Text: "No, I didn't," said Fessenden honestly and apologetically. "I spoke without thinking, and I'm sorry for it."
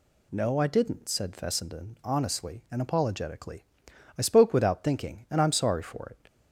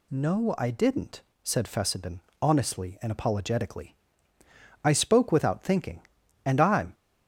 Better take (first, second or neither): first